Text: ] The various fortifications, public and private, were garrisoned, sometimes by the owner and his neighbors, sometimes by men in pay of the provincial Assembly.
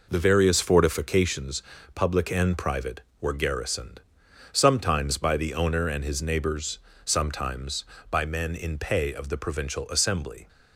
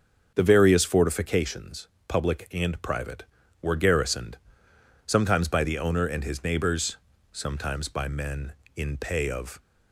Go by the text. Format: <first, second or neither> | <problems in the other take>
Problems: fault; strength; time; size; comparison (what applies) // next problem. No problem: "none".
first | starts louder than the rest; until 1.3 s; 6.5 dB // stops before "the provincial Assembly"; at 9.6 s